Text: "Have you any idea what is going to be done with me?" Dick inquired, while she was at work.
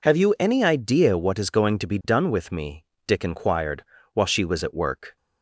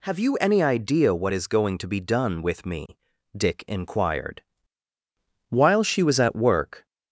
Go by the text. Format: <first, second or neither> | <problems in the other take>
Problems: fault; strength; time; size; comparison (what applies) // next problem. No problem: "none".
neither | none